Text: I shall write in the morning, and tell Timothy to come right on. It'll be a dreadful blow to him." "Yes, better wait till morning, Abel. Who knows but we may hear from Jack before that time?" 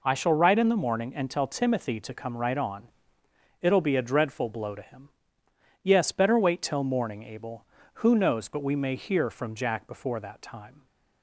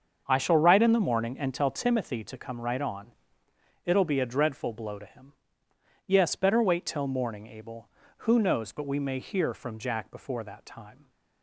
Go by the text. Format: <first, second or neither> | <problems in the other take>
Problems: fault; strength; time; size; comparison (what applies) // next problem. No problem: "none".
first | starts louder than the rest; until 2.0 s; 7 dB